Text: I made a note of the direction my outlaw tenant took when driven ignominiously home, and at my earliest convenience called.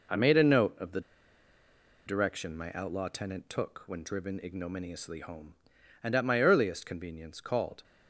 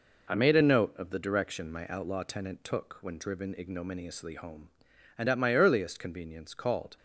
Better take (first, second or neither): second